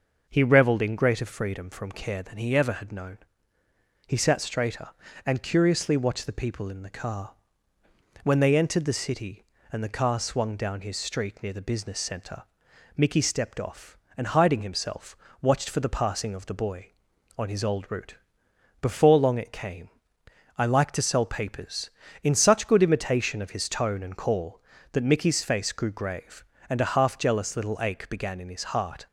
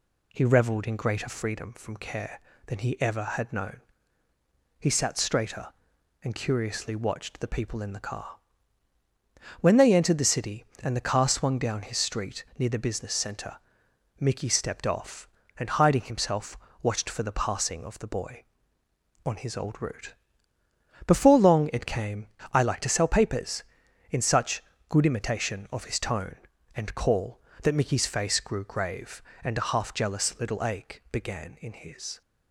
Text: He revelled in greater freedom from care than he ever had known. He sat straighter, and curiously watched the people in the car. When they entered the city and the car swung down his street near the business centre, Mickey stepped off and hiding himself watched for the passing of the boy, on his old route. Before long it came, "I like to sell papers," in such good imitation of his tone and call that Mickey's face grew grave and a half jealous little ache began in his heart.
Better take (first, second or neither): first